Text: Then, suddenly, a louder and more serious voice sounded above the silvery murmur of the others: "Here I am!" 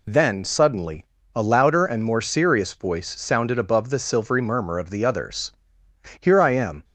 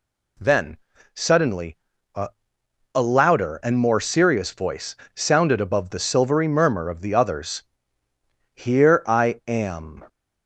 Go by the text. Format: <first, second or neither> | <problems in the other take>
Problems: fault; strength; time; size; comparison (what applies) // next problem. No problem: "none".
first | says "a" twice; at 2.9 s // pauses between "voice" and "sounded"; slight; at 4.9 s; 0.22 s long